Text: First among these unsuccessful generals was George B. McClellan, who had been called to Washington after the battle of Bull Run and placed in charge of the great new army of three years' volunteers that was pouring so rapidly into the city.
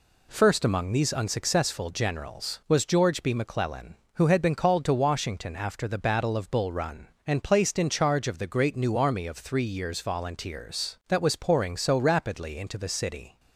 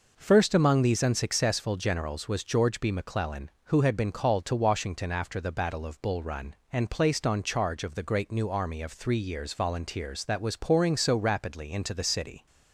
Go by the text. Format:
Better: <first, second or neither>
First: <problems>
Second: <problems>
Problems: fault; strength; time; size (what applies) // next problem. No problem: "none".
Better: first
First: none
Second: says "on" for "in"; at 7.2 s